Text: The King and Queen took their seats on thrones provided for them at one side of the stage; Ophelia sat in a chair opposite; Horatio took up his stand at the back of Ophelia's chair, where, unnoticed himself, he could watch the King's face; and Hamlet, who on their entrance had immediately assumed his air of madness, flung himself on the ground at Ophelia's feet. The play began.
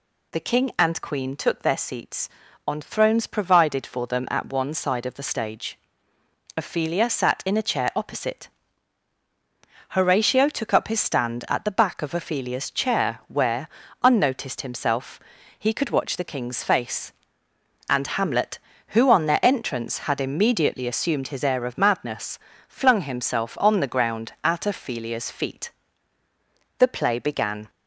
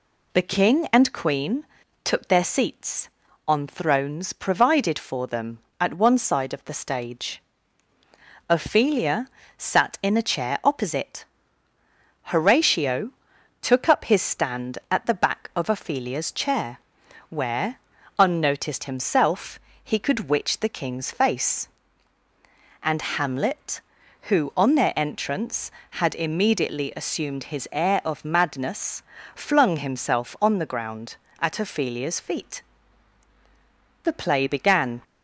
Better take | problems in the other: first | pauses between "Queen" and "took"; at 1.6 s; 0.40 s long // pauses between "Ophelia" and "sat"; slight; at 9.2 s; 0.32 s long // pauses between "Horatio" and "took"; noticeable; at 13.1 s; 0.50 s long // says "witch" for "watch"; at 20.2 s // pauses between "and" and "Hamlet"; slight; at 23.0 s; 0.16 s long

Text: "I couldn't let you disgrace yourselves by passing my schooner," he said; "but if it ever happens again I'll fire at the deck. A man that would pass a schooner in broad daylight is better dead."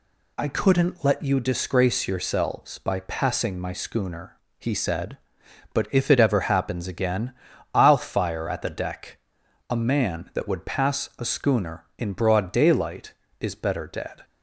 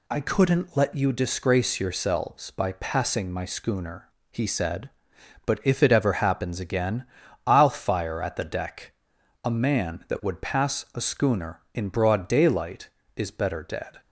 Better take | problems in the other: neither | pauses between "again" and "I'll"; the same in both

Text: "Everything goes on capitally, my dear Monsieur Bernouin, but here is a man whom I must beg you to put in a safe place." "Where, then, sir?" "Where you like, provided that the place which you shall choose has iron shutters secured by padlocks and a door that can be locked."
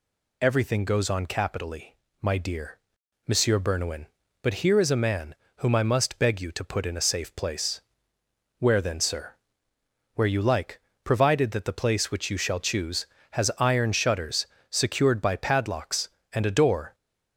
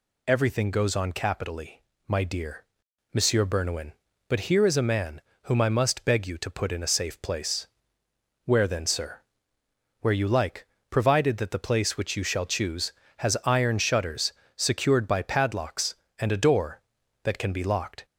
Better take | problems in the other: second | pauses between "dear" and "Monsieur"; noticeable; at 2.7 s; 0.46 s long; noticeable in the second // pauses between "man" and "whom"; slight; at 5.3 s; 0.24 s long; slight in the second // pauses between "shutters" and "secured"; slight; at 14.4 s; 0.24 s long; slight in the second // stops before "that can be locked"; at 16.9 s

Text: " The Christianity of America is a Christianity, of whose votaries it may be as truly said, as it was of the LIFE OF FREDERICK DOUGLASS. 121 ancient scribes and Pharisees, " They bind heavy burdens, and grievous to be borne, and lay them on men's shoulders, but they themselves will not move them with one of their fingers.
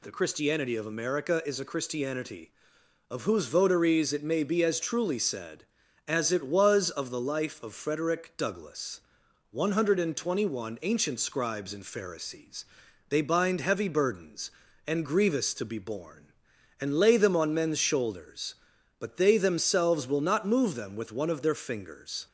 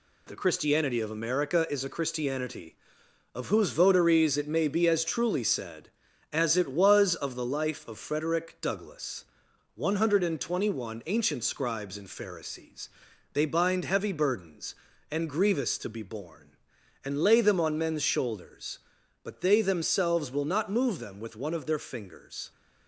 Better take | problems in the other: first | gets quieter; noticeable; throughout; 6 dB

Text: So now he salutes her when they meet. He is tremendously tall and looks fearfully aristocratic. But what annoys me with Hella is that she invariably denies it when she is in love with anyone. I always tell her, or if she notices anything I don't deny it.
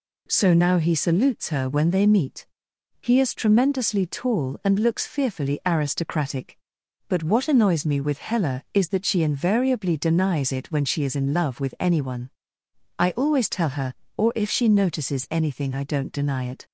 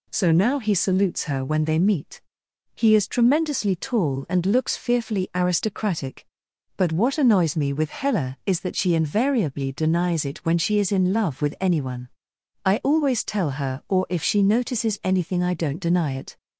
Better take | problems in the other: neither | none

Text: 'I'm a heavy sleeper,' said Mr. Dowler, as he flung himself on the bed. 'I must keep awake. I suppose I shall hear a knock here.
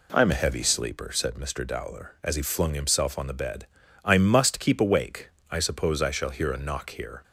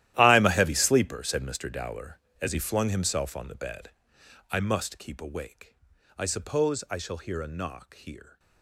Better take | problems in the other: first | gets quieter; strong; throughout; 16.5 dB

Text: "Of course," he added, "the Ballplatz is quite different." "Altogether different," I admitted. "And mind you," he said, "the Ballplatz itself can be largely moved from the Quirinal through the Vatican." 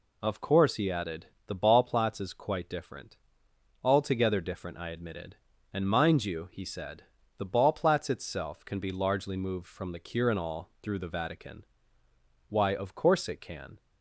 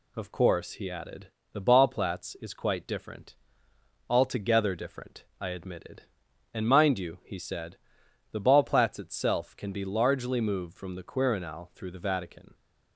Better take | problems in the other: second | goes on to say "Why of course it can"; noticeable; from 12.4 s on; 1.3 s long

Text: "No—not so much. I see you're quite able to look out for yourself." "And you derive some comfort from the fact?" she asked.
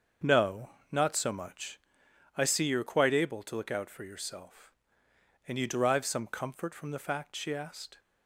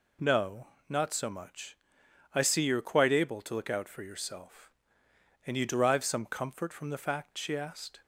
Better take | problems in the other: second | starts louder than the rest; until 2.0 s; 6.5 dB

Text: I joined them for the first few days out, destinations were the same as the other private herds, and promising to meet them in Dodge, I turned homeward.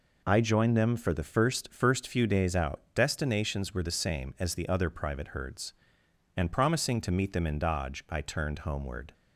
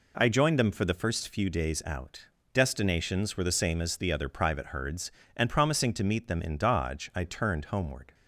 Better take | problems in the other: second | says "first" twice; at 1.7 s

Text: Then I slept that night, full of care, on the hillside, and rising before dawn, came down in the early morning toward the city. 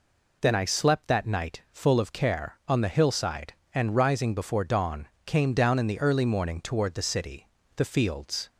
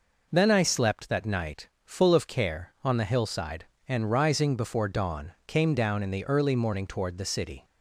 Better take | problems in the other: second | goes on to say "The fields"; noticeable; from 7.7 s on; 0.74 s long

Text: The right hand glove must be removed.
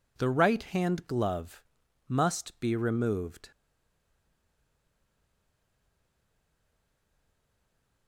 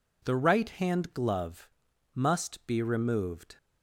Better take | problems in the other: second | pauses between "glove" and "must"; noticeable; at 1.6 s; 0.48 s long; noticeable in the second // stays silent after the last word; strong; from 3.5 s on; 4.5 s long

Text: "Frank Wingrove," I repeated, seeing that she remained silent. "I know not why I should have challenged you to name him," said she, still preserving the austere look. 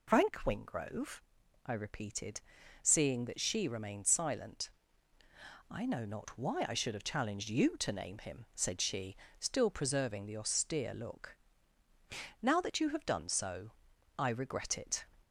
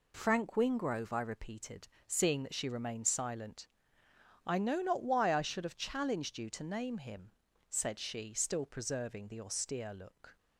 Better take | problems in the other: second | goes on to say "Now that you have done so I regret it"; strong; from 12.4 s on; 2.6 s long

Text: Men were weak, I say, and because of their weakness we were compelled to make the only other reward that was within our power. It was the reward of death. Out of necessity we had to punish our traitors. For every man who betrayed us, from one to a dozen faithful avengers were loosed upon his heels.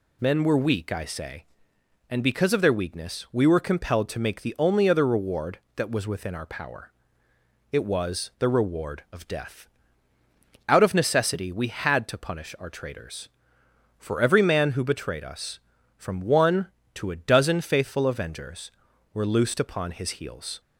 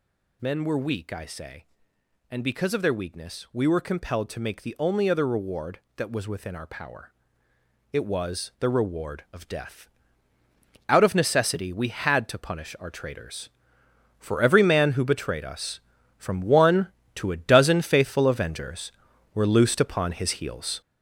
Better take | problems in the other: first | gets louder; throughout; 6 dB

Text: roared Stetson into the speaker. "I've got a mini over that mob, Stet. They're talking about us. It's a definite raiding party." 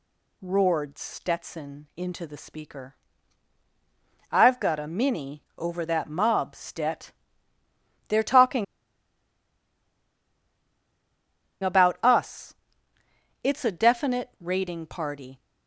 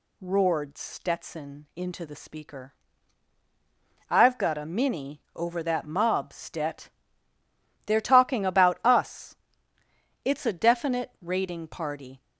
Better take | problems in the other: second | pauses between "talking" and "about"; strong; at 8.6 s; 2.9 s long

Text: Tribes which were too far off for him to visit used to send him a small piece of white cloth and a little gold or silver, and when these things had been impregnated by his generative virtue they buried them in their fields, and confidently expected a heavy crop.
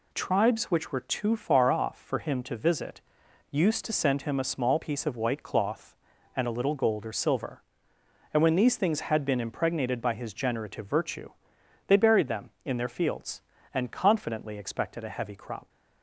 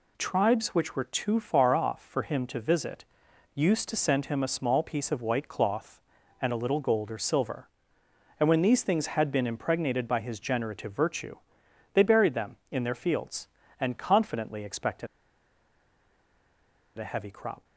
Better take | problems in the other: first | pauses between "visit" and "used"; noticeable; at 3.0 s; 0.48 s long; noticeable in the first // pauses between "virtue" and "they"; noticeable; at 11.3 s; 0.60 s long; noticeable in the first // pauses between "expected" and "a"; strong; at 15.0 s; 1.9 s long

